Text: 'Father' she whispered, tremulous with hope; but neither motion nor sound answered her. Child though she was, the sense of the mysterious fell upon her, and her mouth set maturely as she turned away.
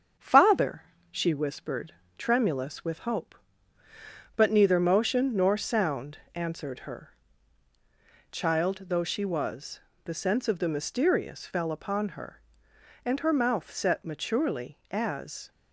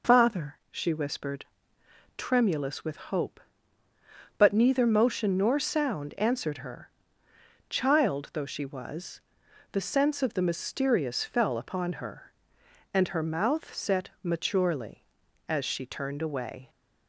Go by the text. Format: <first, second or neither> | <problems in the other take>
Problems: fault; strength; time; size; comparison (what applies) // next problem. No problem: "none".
second | starts louder than the rest; strong; until 1.4 s; 7.5 dB // pauses between "Father" and "she"; slight; at 0.8 s; 0.28 s long // pauses between "sound" and "answered"; slight; at 6.1 s; 0.16 s long // stops before "she turned away"; at 15.5 s